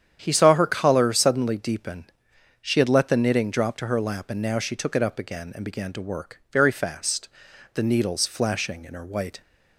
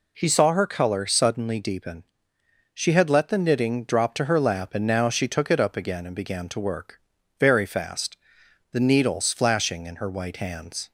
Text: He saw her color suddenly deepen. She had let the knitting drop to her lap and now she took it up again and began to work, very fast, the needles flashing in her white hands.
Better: second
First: starts louder than the rest; strong; until 1.2 s; 9 dB // stops before "hands"; at 9.4 s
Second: none

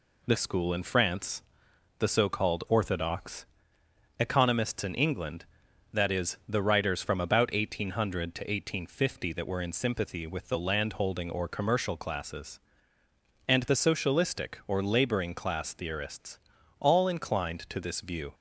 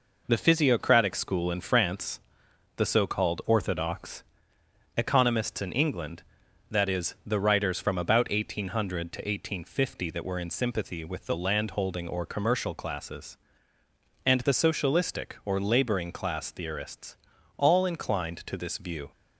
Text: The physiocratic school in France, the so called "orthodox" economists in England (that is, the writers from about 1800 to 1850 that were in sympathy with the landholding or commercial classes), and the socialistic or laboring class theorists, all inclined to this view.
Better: second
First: skips "physiocratic"; at 0.3 s // pauses between "orthodox" and "economists"; noticeable; at 3.4 s; 0.72 s long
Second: pauses between "orthodox" and "economists"; noticeable; at 4.2 s; 0.72 s long

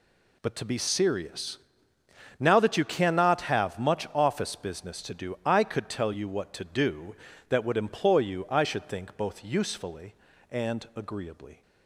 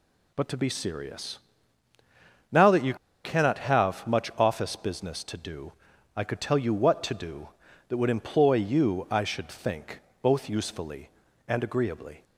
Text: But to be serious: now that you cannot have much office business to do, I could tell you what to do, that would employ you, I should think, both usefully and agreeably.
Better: first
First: none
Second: pauses between "you" and "cannot"; slight; at 2.9 s; 0.29 s long

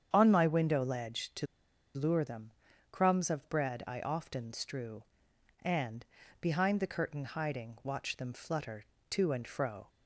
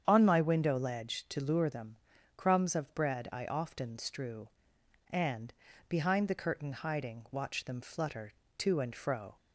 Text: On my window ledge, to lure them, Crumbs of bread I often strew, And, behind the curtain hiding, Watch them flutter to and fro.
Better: second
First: starts louder than the rest; strong; until 1.1 s; 8 dB // pauses between "to" and "lure"; noticeable; at 1.4 s; 0.49 s long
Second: starts louder than the rest; strong; until 1.0 s; 8 dB

